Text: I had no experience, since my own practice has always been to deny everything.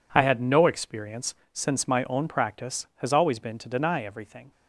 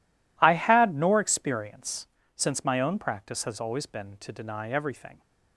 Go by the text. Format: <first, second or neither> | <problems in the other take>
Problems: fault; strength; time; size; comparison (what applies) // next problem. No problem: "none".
first | says "nor" for "no"; at 0.9 s